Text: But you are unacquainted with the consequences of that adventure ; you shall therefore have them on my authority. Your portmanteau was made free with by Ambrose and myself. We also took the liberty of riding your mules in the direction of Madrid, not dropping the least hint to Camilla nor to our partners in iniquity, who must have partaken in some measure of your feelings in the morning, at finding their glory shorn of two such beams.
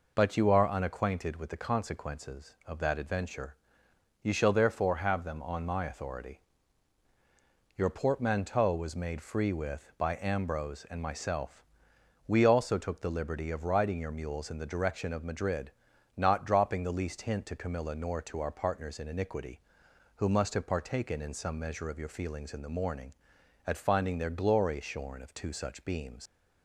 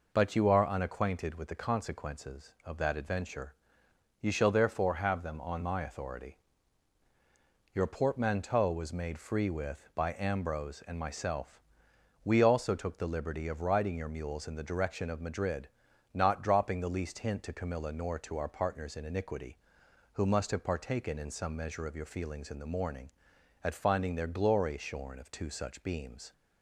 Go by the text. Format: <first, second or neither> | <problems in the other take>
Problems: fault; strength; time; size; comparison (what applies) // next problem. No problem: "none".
second | leaves "beams" unfinished; at 26.2 s; 80 ms